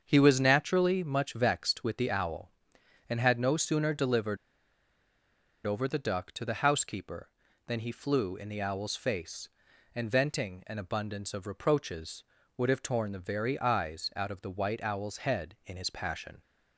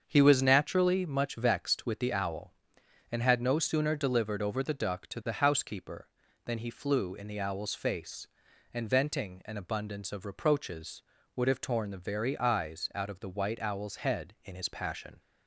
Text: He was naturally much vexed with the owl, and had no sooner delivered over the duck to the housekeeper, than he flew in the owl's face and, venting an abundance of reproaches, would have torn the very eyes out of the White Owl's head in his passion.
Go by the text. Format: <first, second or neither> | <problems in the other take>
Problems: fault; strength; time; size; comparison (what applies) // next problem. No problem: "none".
second | starts louder than the rest; until 1.0 s; 7 dB; also in the second // pauses between "delivered" and "over"; strong; at 4.3 s; 1.2 s long